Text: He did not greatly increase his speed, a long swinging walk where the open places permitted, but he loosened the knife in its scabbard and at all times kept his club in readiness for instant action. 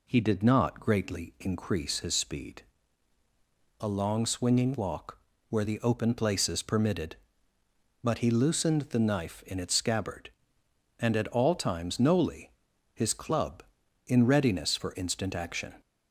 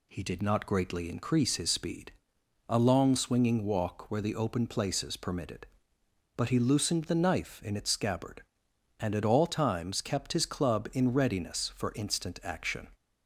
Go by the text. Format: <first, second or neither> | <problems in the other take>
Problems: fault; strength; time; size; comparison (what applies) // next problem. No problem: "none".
second | pauses between "walk" and "where"; slight; at 5.1 s; 0.30 s long // says "noli" for "kept"; at 11.9 s